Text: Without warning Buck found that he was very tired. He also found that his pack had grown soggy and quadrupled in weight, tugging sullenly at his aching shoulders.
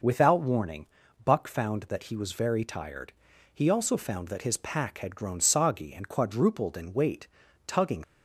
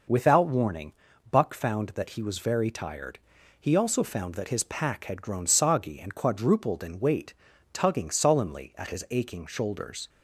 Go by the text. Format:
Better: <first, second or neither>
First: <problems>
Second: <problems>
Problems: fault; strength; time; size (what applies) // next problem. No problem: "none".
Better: second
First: pauses between "warning" and "Buck"; at 0.8 s; 0.38 s long // stops before "sullenly at his aching shoulders"; at 8.0 s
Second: pauses between "warning" and "Buck"; at 0.9 s; 0.38 s long